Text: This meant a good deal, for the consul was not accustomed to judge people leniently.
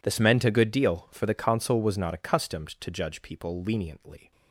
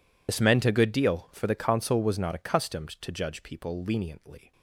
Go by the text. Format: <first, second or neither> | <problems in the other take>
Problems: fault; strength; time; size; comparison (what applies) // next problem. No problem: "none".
first | loses the start of "This"; at 0.2 s; 50 ms